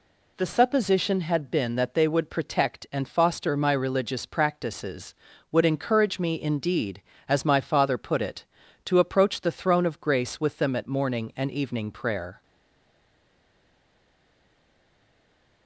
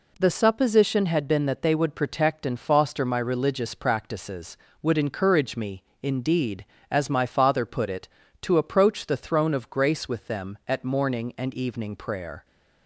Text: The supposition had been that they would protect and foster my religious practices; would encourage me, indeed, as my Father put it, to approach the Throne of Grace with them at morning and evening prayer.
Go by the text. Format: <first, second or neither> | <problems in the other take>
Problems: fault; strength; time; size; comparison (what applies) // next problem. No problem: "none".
second | stays silent after the last word; strong; from 12.4 s on; 3.2 s long